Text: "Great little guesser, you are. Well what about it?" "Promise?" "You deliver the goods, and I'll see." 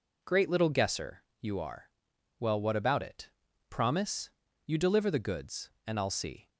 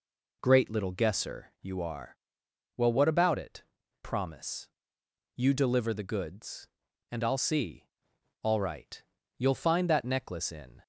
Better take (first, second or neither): first